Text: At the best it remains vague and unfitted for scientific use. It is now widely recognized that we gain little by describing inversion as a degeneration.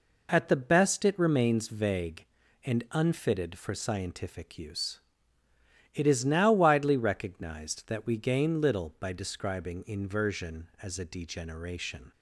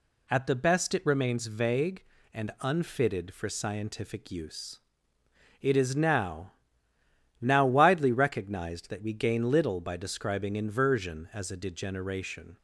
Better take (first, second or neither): first